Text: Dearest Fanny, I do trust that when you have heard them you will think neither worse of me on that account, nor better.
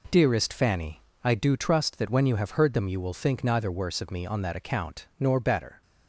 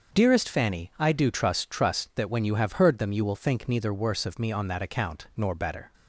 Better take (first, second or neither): first